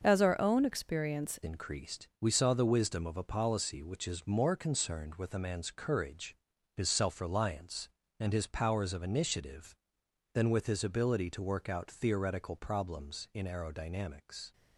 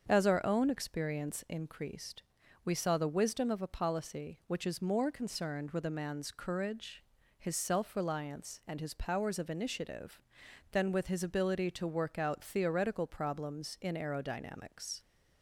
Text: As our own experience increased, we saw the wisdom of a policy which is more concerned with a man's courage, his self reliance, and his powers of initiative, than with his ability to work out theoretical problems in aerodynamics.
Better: second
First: starts louder than the rest; until 1.0 s; 6.5 dB // changes voice at "increased"; from 1.4 s on; 13.1 s long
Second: starts louder than the rest; strong; until 1.0 s; 7 dB

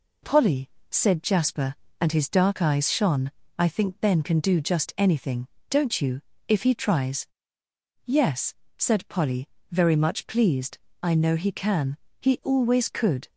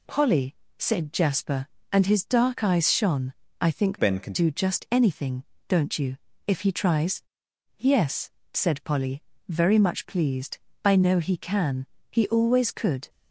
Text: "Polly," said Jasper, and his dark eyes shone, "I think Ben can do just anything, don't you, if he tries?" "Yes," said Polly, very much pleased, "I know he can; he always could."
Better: first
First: none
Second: changes voice from "Ben" to "can"; from 3.9 to 4.3 s; 0.4 s long

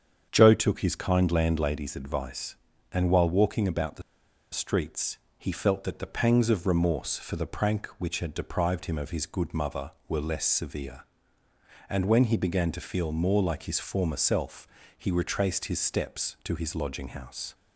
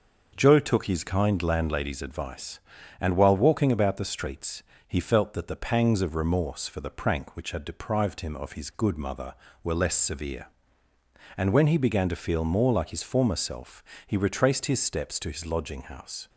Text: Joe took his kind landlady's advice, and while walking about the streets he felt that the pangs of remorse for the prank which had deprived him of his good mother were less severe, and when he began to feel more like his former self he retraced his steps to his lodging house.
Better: second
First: starts louder than the rest; strong; until 1.3 s; 7.5 dB // pauses between "the" and "streets"; noticeable; at 4.0 s; 0.50 s long // pauses between "streets" and "he"; slight; at 5.1 s; 0.18 s long // pauses between "self" and "he"; slight; at 14.6 s; 0.28 s long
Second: starts louder than the rest; noticeable; until 1.3 s; 6 dB // pauses between "streets" and "he"; slight; at 4.6 s; 0.24 s long // pauses between "self" and "he"; slight; at 13.8 s; 0.24 s long

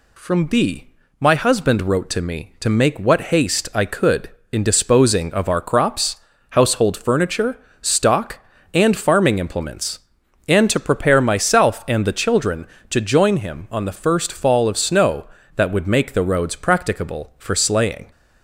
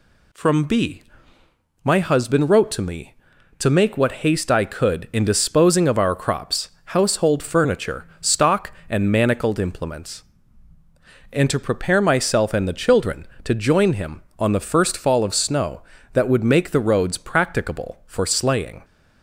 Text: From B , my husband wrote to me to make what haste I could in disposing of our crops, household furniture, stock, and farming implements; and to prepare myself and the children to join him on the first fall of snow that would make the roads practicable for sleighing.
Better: first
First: none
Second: says "manacled" for "farming"; at 9.1 s

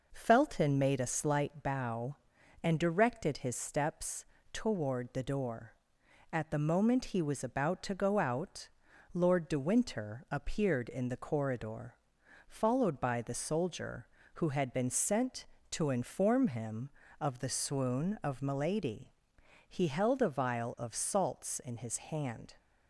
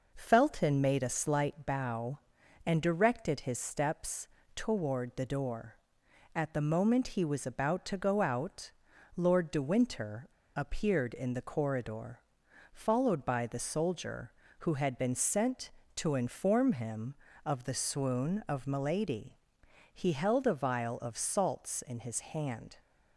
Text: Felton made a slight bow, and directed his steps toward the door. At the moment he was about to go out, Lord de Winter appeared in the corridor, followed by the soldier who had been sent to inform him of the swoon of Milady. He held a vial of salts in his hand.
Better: first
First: pauses between "steps" and "toward"; slight; at 4.2 s; 0.28 s long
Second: pauses between "steps" and "toward"; slight; at 4.2 s; 0.28 s long // pauses between "Winter" and "appeared"; slight; at 10.2 s; 0.29 s long

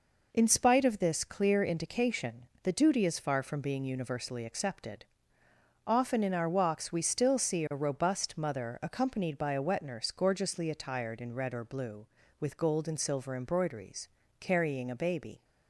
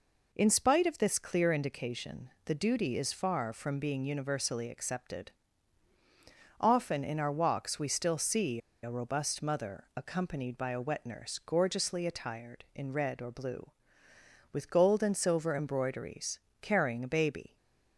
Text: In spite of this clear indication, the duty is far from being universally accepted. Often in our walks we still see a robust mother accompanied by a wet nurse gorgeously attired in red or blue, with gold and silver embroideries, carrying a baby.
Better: first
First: none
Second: pauses between "see" and "a"; slight; at 8.5 s; 0.25 s long // stays silent after the last word; slight; from 17.4 s on; 0.5 s long

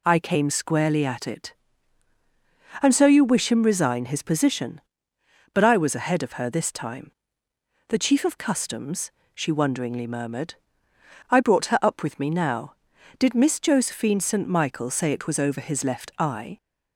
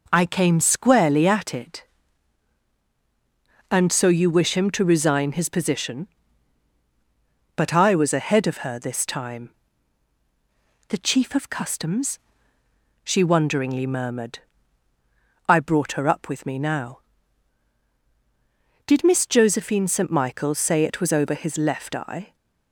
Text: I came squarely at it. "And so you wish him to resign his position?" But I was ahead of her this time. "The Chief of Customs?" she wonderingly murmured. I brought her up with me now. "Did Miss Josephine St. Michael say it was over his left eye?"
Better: second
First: skips "to"; at 3.6 s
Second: none

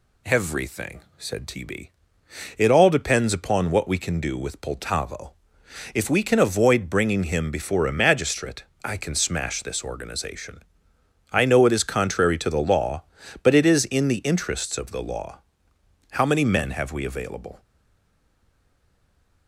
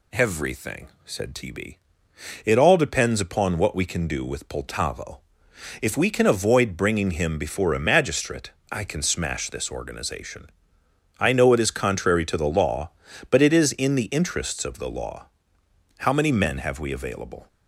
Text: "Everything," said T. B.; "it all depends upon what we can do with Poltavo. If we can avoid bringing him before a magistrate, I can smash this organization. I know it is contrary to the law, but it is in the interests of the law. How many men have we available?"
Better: second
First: stays silent after the last word; noticeable; from 17.5 s on; 1.9 s long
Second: none

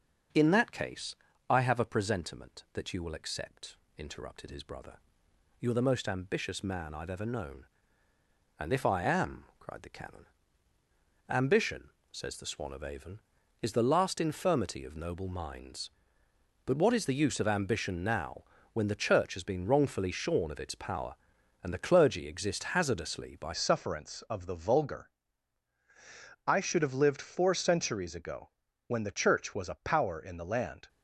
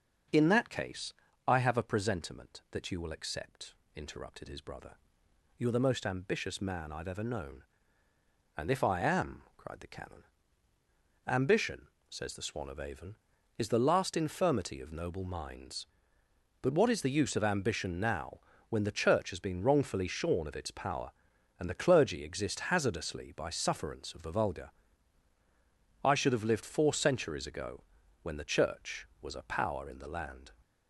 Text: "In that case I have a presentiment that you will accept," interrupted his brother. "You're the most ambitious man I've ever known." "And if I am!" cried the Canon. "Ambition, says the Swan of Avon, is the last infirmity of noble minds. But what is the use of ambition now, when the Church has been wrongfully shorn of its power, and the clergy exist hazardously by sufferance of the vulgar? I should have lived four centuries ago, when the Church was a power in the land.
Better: second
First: starts louder than the rest; noticeable; until 1.6 s; 6 dB // pauses between "case" and "I"; slight; at 1.1 s; 0.32 s long // changes voice at "sufferance"; from 23.5 s on; 7.3 s long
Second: starts louder than the rest; noticeable; until 1.6 s; 6 dB // pauses between "case" and "I"; slight; at 1.1 s; 0.32 s long

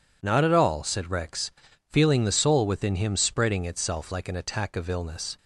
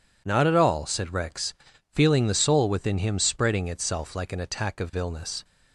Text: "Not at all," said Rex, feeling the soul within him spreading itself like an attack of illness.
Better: neither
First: none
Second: none

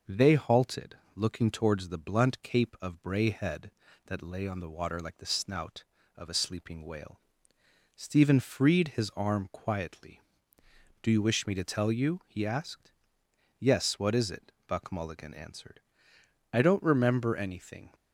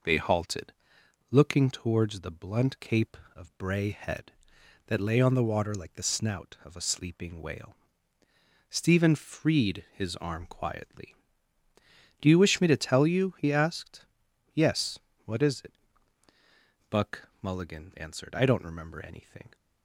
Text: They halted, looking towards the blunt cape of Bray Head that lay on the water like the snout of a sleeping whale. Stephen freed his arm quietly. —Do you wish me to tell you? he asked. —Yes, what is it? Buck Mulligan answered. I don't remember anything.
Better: neither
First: none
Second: none

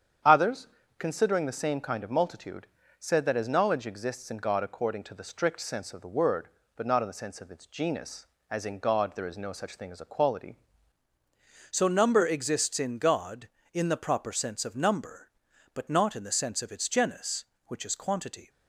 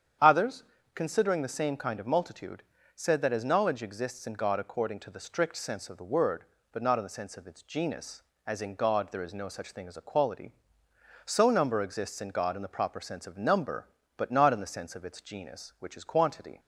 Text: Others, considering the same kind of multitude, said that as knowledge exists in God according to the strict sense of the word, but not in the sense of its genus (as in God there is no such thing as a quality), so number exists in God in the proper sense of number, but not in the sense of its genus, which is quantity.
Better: second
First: starts louder than the rest; strong; until 1.5 s; 8.5 dB // changes voice at "so"; from 11.6 s on; 6.8 s long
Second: starts louder than the rest; strong; until 1.5 s; 8.5 dB

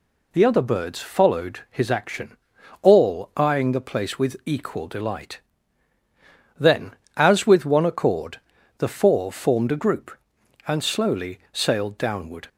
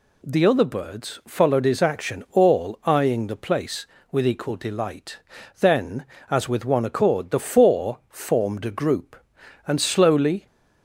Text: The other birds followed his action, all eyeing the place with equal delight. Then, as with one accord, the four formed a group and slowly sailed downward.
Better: first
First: none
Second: stops before "sailed downward"; at 10.4 s

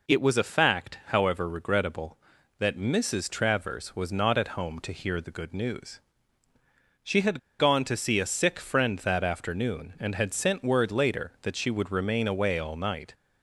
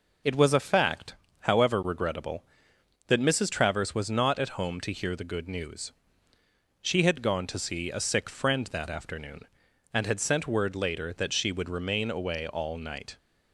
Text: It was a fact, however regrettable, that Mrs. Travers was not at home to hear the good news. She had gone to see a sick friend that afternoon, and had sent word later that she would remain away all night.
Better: second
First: pauses between "had" and "gone"; slight; at 7.3 s; 0.19 s long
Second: none

